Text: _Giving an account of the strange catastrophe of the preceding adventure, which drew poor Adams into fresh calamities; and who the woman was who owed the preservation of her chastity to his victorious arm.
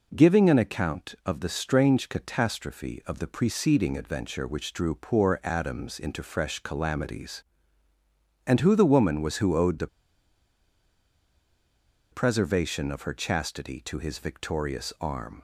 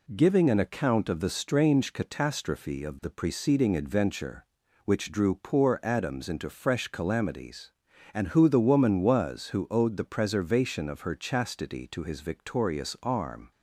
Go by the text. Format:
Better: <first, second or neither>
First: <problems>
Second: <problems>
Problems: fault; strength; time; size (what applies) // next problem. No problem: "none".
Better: second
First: pauses between "the" and "preservation"; strong; at 9.8 s; 2.2 s long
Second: none